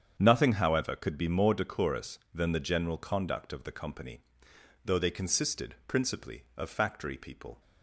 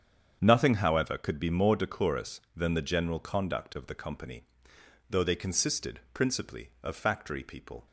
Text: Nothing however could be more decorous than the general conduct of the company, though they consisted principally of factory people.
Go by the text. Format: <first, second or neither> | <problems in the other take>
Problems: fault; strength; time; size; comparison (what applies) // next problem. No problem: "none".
neither | starts louder than the rest; strong; the same in both